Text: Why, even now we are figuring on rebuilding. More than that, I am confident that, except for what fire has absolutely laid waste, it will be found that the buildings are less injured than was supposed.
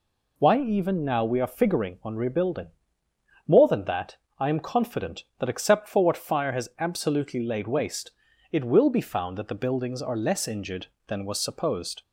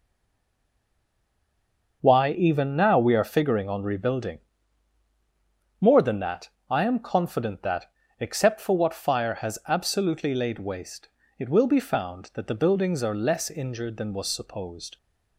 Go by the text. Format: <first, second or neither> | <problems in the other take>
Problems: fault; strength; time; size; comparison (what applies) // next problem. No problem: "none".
first | stays silent before the first word; noticeable; until 2.0 s; 2.0 s long